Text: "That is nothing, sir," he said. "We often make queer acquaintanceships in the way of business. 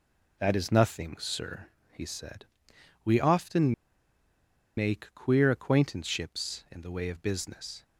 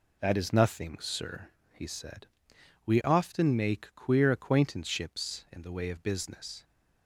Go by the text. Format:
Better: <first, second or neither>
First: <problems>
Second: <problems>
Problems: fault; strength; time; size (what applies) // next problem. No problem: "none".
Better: second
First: pauses between "often" and "make"; at 3.7 s; 1.0 s long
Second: none